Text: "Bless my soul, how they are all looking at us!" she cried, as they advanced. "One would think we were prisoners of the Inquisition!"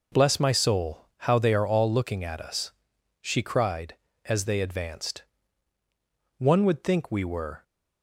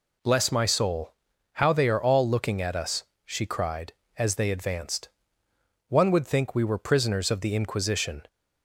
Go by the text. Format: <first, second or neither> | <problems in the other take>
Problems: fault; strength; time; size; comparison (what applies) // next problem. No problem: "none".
second | stops before "prisoners of the Inquisition"; at 7.6 s